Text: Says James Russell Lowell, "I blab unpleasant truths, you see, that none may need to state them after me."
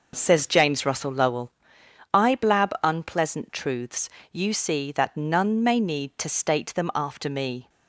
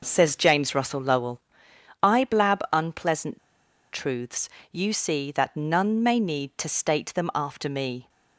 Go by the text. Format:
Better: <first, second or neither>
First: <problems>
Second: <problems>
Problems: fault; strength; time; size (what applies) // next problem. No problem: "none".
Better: first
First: none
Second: pauses between "unpleasant" and "truths"; noticeable; at 3.3 s; 0.53 s long